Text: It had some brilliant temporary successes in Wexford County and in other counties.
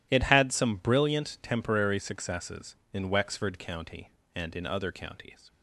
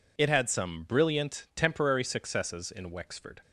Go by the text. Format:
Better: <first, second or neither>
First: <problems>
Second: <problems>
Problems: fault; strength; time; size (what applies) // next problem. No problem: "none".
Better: first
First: none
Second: stops before "County and in other counties"; at 3.4 s